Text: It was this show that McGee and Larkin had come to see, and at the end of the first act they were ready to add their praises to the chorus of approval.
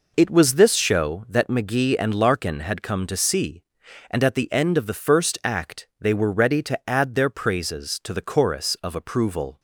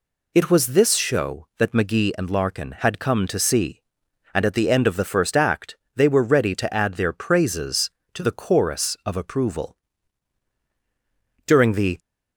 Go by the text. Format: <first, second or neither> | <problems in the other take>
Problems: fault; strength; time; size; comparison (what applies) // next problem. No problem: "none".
first | pauses between "act" and "they"; slight; at 5.7 s; 0.20 s long // goes on to say "During the"; from 11.4 s on; 0.52 s long